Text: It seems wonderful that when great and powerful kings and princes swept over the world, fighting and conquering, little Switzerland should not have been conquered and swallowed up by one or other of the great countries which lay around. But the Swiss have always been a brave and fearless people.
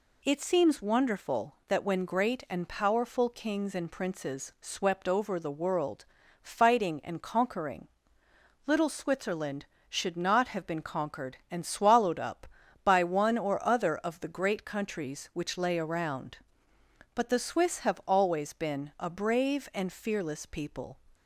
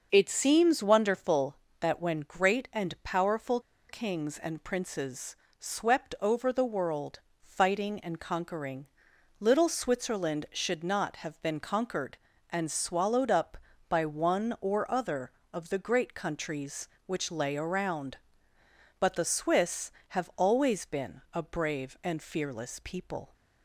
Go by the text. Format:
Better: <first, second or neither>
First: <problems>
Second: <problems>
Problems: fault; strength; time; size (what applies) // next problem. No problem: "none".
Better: first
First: none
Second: starts louder than the rest; until 1.1 s; 6 dB // pauses between "powerful" and "kings"; slight; at 3.5 s; 0.29 s long // pauses between "princes" and "swept"; slight; at 5.3 s; 0.24 s long